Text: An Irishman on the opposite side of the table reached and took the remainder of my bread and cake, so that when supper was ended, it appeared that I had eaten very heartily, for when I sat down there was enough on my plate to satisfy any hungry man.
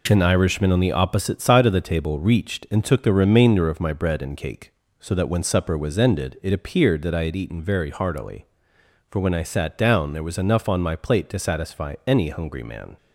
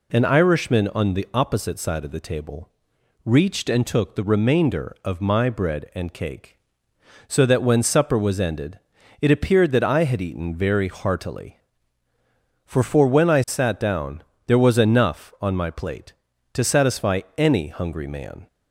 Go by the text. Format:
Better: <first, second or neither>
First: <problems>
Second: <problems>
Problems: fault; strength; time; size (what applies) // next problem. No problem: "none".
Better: first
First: none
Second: pauses between "table" and "reached"; noticeable; at 2.6 s; 0.54 s long // says "for" twice; at 12.8 s // pauses between "down" and "there"; slight; at 14.2 s; 0.24 s long